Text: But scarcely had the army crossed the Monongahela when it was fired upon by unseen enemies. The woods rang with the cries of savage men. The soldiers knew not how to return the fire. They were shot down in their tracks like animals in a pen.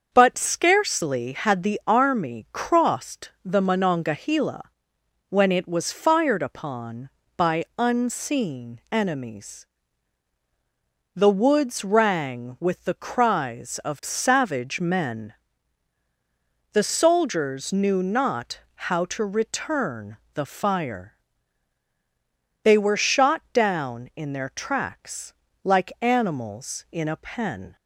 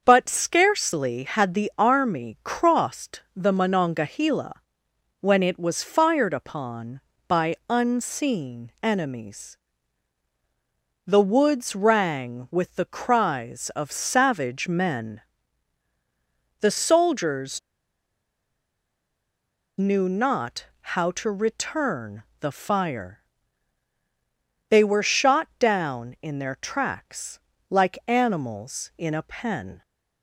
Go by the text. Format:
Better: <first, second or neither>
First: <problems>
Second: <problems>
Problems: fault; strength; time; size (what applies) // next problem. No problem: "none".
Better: first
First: starts louder than the rest; until 1.1 s; 6.5 dB // pauses between "Monongahela" and "when"; noticeable; at 4.6 s; 0.66 s long // pauses between "not" and "how"; slight; at 18.5 s; 0.16 s long // pauses between "return" and "the"; slight; at 20.1 s; 0.18 s long // pauses between "tracks" and "like"; slight; at 25.3 s; 0.32 s long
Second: starts louder than the rest; until 1.0 s; 6.5 dB // pauses between "Monongahela" and "when"; noticeable; at 4.5 s; 0.66 s long // pauses between "soldiers" and "knew"; strong; at 17.5 s; 2.1 s long // pauses between "not" and "how"; slight; at 20.6 s; 0.16 s long // pauses between "return" and "the"; slight; at 22.2 s; 0.18 s long // pauses between "tracks" and "like"; slight; at 27.3 s; 0.32 s long